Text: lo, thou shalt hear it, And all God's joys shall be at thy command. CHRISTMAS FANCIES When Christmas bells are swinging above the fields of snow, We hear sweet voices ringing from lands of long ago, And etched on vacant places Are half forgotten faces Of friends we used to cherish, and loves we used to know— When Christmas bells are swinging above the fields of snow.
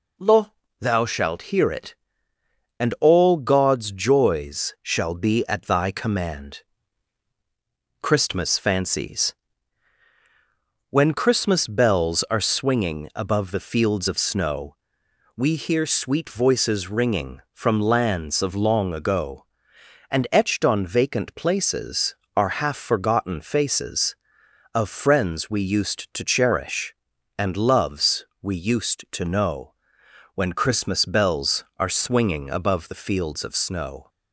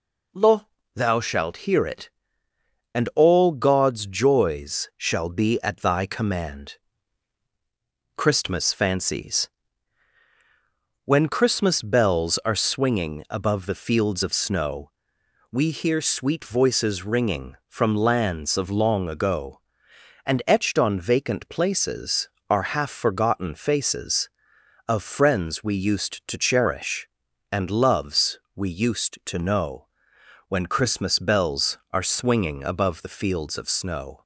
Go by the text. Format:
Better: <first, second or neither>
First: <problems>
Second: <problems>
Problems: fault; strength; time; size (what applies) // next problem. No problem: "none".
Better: neither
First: pauses between "FANCIES" and "When"; strong; at 9.3 s; 1.5 s long // pauses between "loves" and "we"; slight; at 28.2 s; 0.16 s long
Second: pauses between "FANCIES" and "When"; strong; at 9.4 s; 1.5 s long // pauses between "loves" and "we"; slight; at 28.4 s; 0.16 s long